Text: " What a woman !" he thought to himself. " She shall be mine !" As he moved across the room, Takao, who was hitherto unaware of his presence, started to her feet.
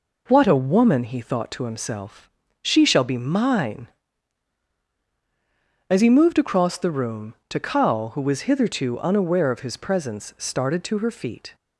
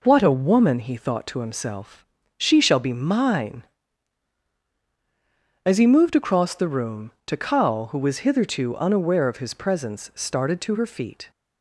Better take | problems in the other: neither | none

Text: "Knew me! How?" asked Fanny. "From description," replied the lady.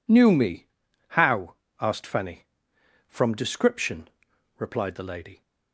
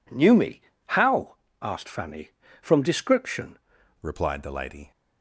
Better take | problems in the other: first | changes voice at "replied"; from 4.0 s on; 0.9 s long

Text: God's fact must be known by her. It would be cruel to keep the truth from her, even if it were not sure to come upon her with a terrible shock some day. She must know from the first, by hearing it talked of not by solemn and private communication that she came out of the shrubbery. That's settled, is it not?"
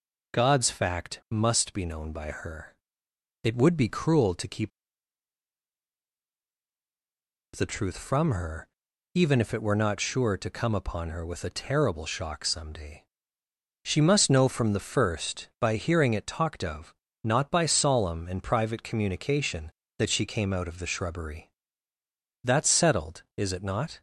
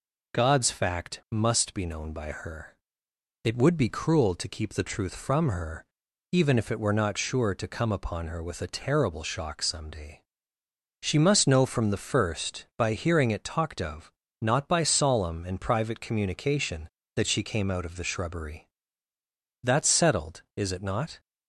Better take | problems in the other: second | pauses between "keep" and "the"; strong; at 4.7 s; 2.8 s long // pauses between "of" and "not"; slight; at 16.9 s; 0.30 s long; slight in the second

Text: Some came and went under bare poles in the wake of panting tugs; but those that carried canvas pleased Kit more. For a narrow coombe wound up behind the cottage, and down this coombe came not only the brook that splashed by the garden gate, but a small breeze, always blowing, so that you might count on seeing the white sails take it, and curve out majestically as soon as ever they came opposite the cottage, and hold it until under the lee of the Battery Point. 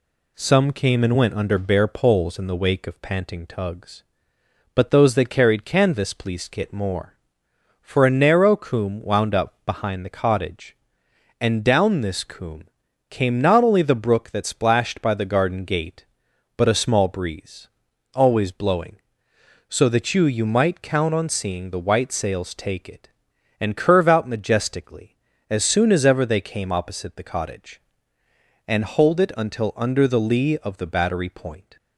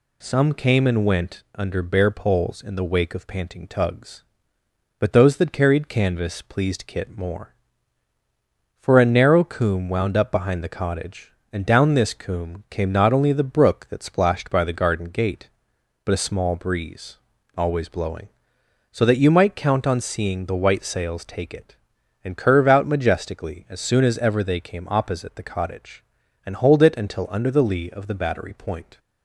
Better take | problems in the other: second | pauses between "coombe" and "came"; at 12.6 s; 0.42 s long // says "you" twice; at 20.2 s

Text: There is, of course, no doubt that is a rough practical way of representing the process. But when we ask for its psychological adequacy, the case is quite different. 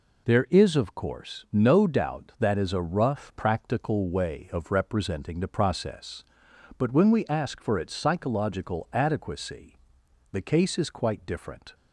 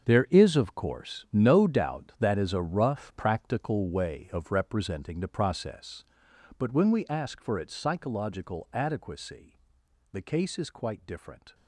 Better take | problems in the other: first | gets quieter; strong; throughout; 13.5 dB

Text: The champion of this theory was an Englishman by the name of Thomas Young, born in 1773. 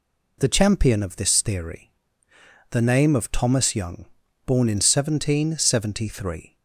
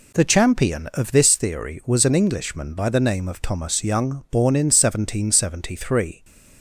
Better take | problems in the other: second | skips "was an Englishman by"; at 2.3 s

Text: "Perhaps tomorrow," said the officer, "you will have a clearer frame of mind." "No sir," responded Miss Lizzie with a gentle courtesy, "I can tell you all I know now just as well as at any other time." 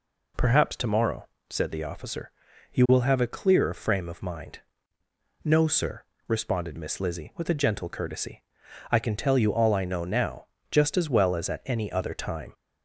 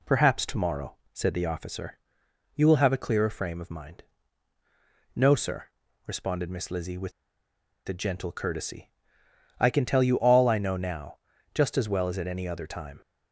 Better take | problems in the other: first | pauses between "with" and "a"; noticeable; at 7.1 s; 0.75 s long // pauses between "now" and "just"; slight; at 11.1 s; 0.36 s long; slight in the first

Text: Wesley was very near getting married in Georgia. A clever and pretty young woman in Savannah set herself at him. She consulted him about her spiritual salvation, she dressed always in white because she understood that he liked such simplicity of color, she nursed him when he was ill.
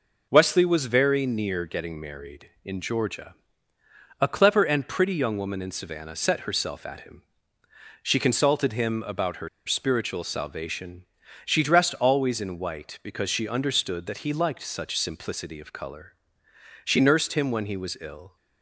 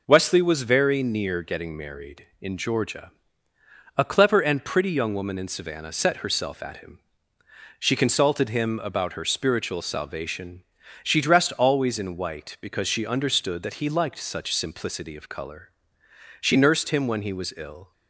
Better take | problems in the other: second | pauses between "her" and "spiritual"; slight; at 9.4 s; 0.18 s long

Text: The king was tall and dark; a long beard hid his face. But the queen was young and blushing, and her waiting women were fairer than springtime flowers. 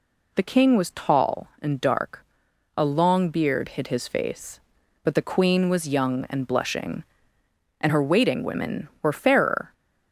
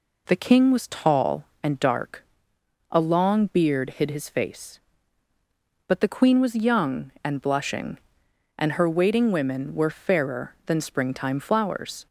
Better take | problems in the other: second | stops before "than springtime flowers"; at 9.7 s

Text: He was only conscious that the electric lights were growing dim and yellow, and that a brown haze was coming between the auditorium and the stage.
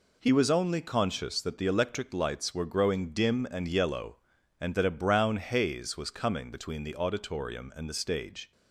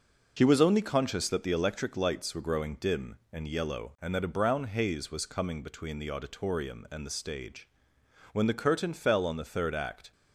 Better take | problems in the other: first | goes on to say "When the curtain fell on the third act"; strong; from 8.3 s on; 1.7 s long

